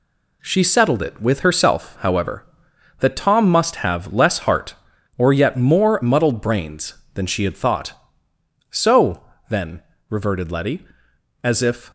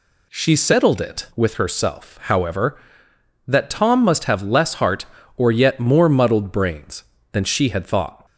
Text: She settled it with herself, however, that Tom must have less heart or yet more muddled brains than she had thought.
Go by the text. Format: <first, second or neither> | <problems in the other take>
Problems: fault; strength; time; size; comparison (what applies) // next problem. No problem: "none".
second | goes on to say "So then reverted Letty as if"; strong; from 8.7 s on; 3.2 s long